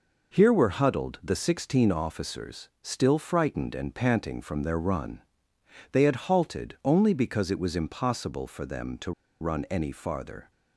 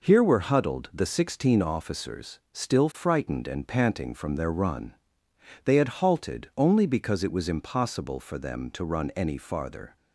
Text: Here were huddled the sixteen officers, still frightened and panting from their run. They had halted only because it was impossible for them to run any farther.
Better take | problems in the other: second | pauses between "to" and "run"; slight; at 9.1 s; 0.29 s long

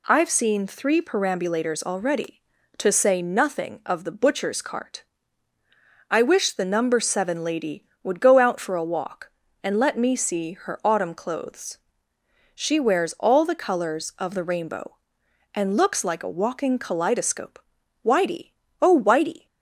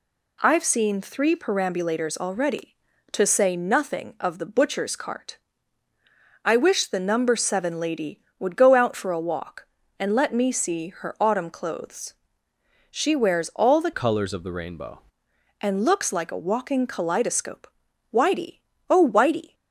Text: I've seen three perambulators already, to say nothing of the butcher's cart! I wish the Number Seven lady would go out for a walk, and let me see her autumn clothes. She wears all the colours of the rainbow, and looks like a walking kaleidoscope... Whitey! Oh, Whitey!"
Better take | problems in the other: first | changes voice from "colours" to "rainbow"; from 13.9 to 14.9 s; 1.0 s long

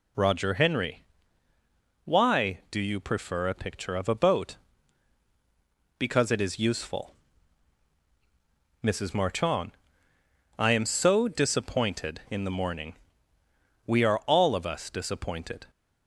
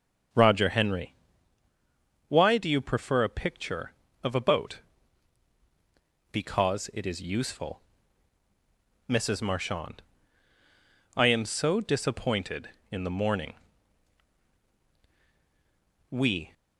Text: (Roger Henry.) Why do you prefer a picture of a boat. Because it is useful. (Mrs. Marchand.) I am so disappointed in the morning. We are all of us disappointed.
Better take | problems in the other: first | starts louder than the rest; strong; until 2.4 s; 7 dB // stops before "are all of us disappointed"; at 16.5 s

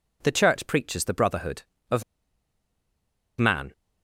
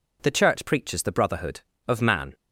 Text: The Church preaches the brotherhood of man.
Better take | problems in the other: second | pauses between "of" and "man"; strong; at 2.0 s; 1.3 s long

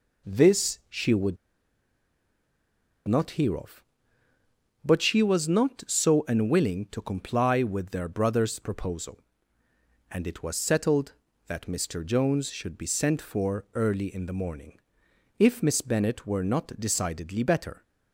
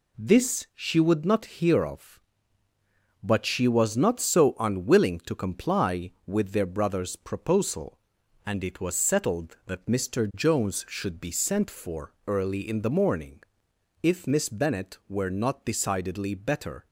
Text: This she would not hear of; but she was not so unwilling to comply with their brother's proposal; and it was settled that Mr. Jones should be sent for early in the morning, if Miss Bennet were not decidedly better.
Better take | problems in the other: second | pauses between "would" and "not"; strong; at 1.3 s; 1.7 s long

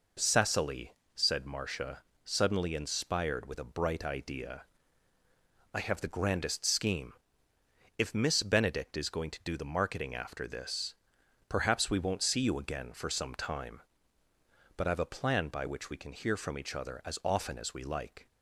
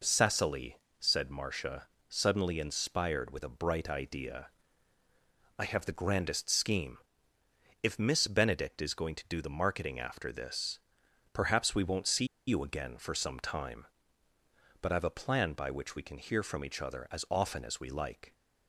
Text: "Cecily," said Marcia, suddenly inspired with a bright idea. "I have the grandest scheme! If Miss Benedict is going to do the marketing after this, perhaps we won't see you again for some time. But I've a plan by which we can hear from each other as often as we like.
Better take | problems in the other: first | pauses between "see" and "you"; slight; at 12.2 s; 0.22 s long

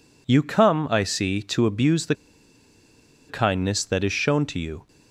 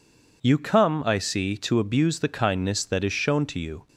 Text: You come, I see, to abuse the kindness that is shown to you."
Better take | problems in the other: second | pauses between "the" and "kindness"; at 2.1 s; 1.1 s long

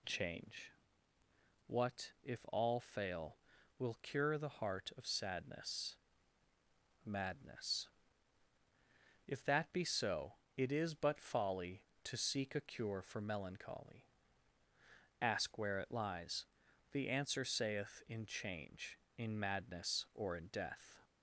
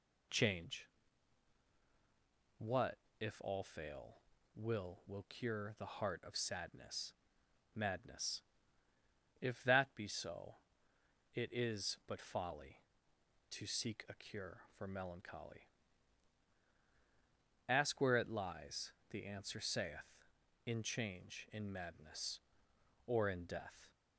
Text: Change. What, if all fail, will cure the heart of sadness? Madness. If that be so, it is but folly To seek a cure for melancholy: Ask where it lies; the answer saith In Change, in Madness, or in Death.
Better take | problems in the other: first | says "will" twice; at 5.0 s

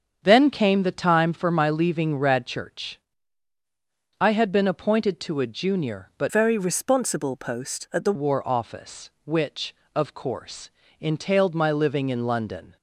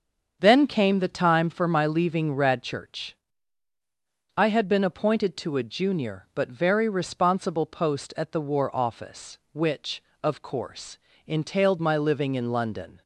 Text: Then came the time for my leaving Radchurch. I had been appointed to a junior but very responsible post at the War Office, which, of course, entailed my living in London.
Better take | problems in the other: second | starts louder than the rest; strong; until 1.2 s; 7.5 dB; also in the second // changes voice from "very" to "the"; from 6.2 to 8.1 s; 1.9 s long

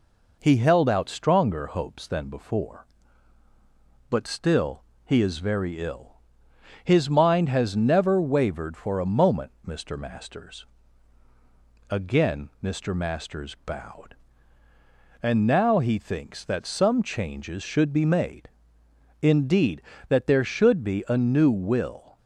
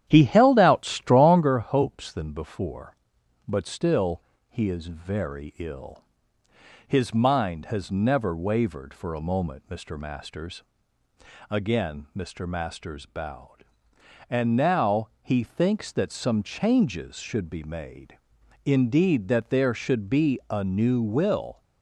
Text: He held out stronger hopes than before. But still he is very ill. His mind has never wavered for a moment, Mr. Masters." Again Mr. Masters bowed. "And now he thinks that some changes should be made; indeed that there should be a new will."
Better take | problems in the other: first | starts louder than the rest; strong; until 1.6 s; 10.5 dB // pauses between "still" and "he"; slight; at 4.2 s; 0.28 s long; slight in the first

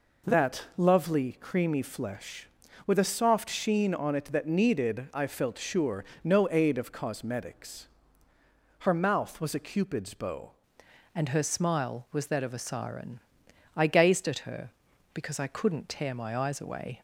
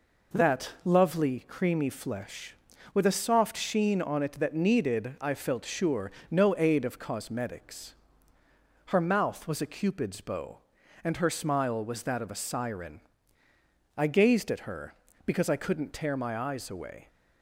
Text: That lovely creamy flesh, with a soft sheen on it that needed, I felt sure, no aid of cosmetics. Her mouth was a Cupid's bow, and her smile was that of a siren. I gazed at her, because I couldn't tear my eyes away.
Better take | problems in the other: second | changes voice at "and"; from 11.1 s on; 5.9 s long

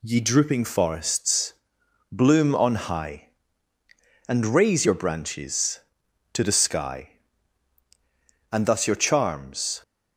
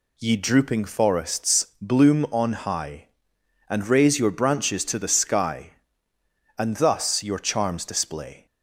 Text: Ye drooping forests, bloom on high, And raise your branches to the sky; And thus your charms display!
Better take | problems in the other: second | stops before "display"; at 9.8 s

